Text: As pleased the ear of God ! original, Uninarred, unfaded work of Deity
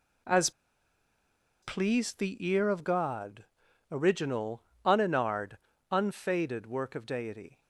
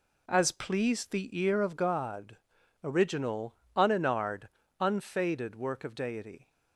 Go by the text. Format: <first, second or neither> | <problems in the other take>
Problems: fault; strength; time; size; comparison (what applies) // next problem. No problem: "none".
second | pauses between "As" and "pleased"; at 0.4 s; 1.1 s long